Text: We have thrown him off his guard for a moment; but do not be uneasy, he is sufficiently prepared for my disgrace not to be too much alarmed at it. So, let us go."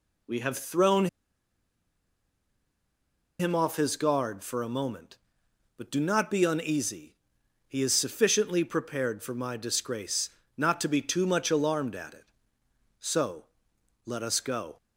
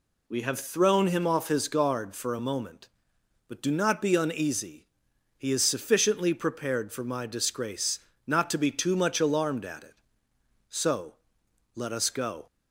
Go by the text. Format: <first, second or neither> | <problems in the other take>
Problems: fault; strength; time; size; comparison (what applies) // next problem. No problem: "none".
second | pauses between "thrown" and "him"; strong; at 1.0 s; 2.3 s long // pauses between "disgrace" and "not"; slight; at 10.2 s; 0.26 s long; slight in the second